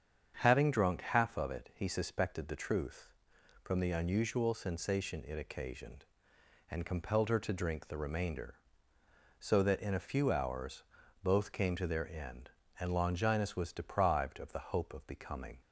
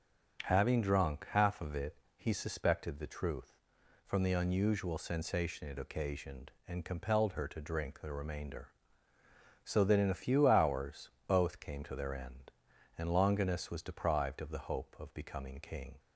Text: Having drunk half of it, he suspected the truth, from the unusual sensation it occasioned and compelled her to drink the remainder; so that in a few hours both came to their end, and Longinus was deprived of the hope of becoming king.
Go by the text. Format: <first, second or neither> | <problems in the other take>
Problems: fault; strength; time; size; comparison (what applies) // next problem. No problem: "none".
second | starts louder than the rest; strong; until 1.3 s; 7.5 dB; strong in the second // pauses between "hours" and "both"; at 10.8 s; 0.40 s long; slight in the second // stops before "king"; at 15.6 s